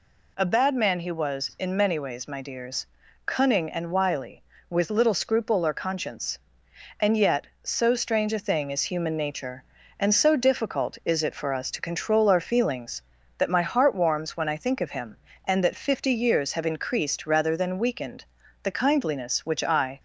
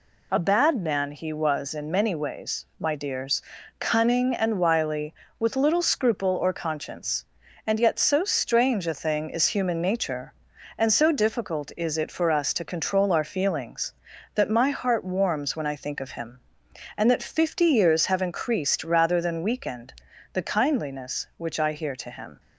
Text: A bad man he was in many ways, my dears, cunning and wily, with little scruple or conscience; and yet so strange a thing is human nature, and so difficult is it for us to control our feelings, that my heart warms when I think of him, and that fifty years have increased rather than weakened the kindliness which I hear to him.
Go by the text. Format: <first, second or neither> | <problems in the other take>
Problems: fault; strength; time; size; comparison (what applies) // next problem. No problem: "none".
second | pauses between "weakened" and "the"; at 18.2 s; 0.40 s long; also in the second // stops before "hear to him"; at 19.9 s